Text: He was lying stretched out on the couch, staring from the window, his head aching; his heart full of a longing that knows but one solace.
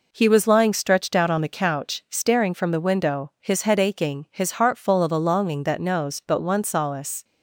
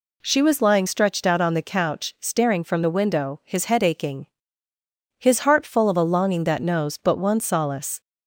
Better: first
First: none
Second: says "She" for "He"; at 0.2 s

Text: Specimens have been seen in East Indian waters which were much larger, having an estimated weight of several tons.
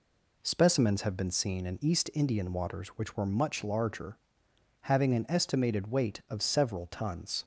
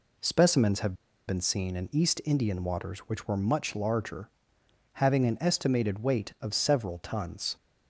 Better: first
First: none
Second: pauses between "have" and "been"; slight; at 0.9 s; 0.32 s long

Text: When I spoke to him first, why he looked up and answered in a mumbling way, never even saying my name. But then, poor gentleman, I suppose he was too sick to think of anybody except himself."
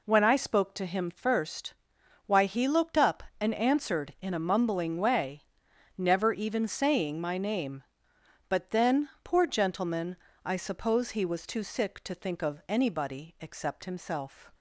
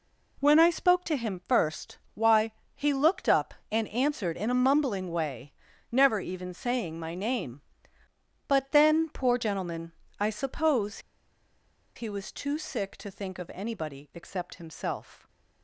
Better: first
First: none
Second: pauses between "why" and "he"; slight; at 2.5 s; 0.20 s long // pauses between "suppose" and "he"; noticeable; at 10.9 s; 0.96 s long

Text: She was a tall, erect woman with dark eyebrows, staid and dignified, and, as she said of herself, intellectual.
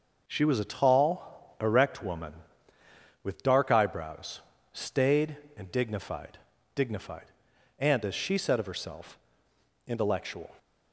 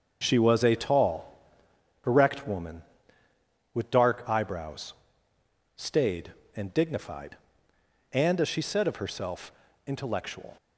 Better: second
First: starts louder than the rest; noticeable; until 1.2 s; 6 dB // says "dignified" twice; at 6.7 s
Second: starts louder than the rest; until 1.2 s; 6.5 dB

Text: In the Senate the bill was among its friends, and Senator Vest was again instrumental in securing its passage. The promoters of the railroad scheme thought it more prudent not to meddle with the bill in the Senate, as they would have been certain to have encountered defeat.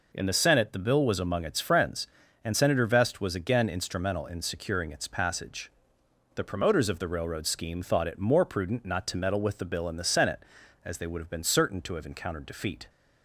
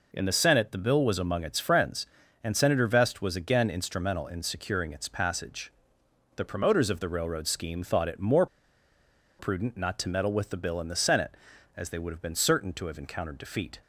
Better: first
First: none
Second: pauses between "more" and "prudent"; noticeable; at 8.4 s; 0.93 s long

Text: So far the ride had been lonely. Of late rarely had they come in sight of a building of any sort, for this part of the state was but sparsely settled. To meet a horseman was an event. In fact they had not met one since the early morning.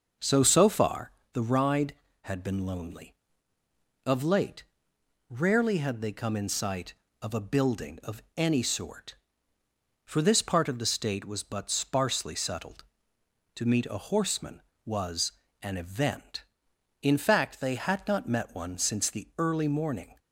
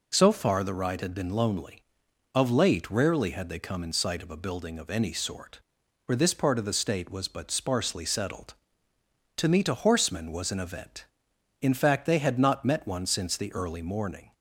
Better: second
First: starts louder than the rest; noticeable; until 1.4 s; 6 dB // says "So" twice; at 0.4 s // pauses between "far" and "the"; slight; at 1.1 s; 0.22 s long // pauses between "late" and "rarely"; noticeable; at 4.6 s; 0.66 s long // pauses between "was" and "an"; slight; at 15.3 s; 0.28 s long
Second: none

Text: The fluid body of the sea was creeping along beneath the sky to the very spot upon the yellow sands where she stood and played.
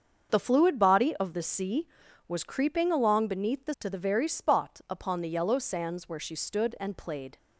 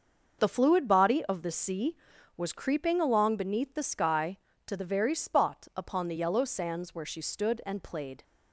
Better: second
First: starts louder than the rest; until 1.3 s; 7 dB // skips "sky"; at 3.7 s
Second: starts louder than the rest; until 1.4 s; 6 dB

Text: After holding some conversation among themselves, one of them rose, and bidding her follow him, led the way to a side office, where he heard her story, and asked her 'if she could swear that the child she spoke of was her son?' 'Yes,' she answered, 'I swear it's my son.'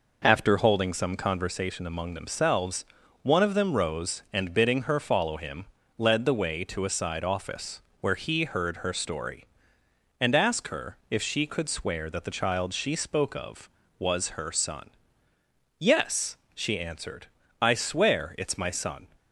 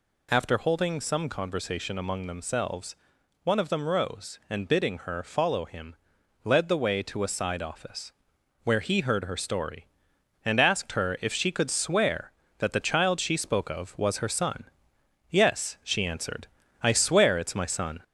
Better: first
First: none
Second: gets louder; slight; throughout; 2.5 dB

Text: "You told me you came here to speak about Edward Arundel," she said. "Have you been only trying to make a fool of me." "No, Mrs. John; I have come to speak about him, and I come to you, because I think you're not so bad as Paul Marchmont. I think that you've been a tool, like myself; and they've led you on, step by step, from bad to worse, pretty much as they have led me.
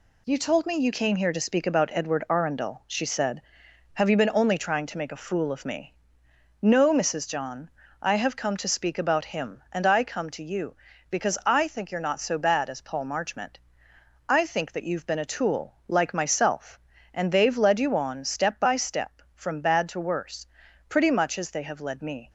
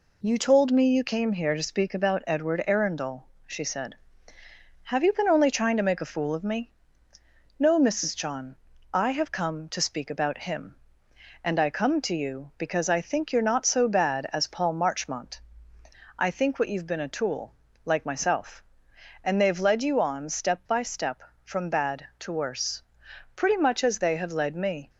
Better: first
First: none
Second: says "what" for "that"; at 16.5 s

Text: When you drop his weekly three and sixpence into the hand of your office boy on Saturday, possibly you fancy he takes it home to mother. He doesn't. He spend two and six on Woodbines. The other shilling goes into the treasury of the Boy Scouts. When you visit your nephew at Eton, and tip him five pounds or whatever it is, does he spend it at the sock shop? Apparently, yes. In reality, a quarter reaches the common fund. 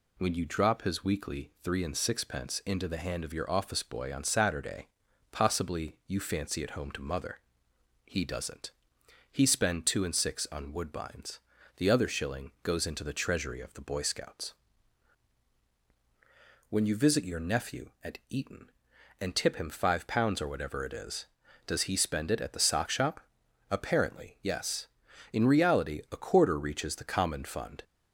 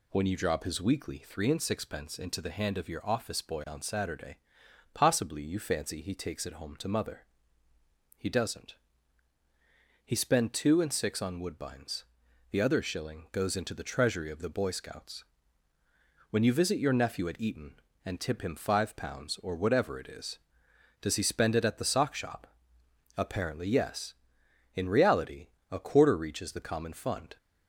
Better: second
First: skips "he takes"; at 6.6 s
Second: none

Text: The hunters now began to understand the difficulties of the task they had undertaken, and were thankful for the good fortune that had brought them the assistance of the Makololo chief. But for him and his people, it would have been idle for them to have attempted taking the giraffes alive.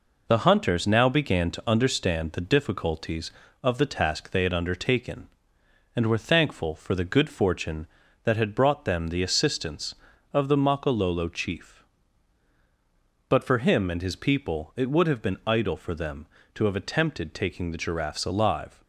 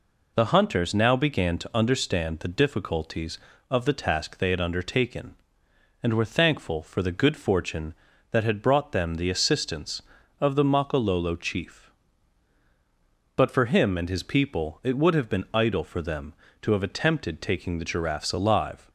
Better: second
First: gets quieter; noticeable; throughout; 4.5 dB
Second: none

